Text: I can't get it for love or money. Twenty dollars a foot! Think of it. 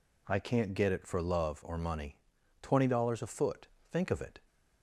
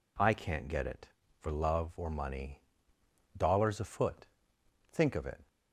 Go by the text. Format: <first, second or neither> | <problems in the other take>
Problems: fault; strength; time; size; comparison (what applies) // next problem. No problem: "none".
first | skips "Twenty"; at 2.9 s